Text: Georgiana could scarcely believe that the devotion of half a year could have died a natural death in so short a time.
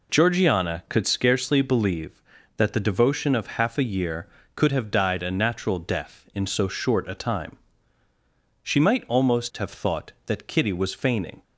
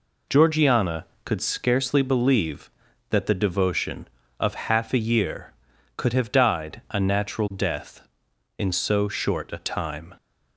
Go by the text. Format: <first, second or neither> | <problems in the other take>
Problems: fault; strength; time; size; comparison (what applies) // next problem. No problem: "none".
second | goes on to say "She might almost have thought that Kitty was feigning"; strong; from 8.6 s on; 2.8 s long